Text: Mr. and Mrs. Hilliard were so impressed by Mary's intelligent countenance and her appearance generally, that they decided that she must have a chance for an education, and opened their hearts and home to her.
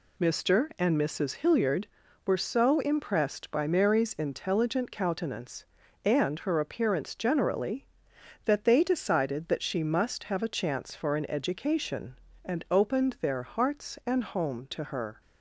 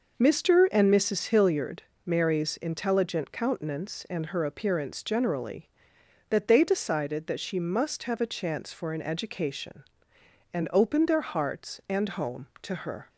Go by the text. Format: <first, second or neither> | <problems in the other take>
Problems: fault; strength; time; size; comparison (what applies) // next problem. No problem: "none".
first | skips "were so impressed by"; at 1.9 s